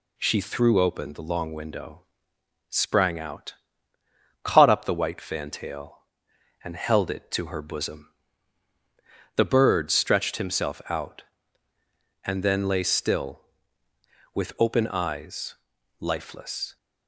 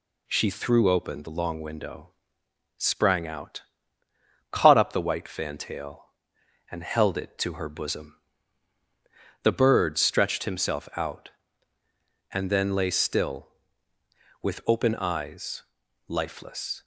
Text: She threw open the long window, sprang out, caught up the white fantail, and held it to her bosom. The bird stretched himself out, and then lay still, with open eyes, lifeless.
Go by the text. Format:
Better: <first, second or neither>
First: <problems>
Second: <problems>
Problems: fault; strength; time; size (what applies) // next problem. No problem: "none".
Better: neither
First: none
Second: none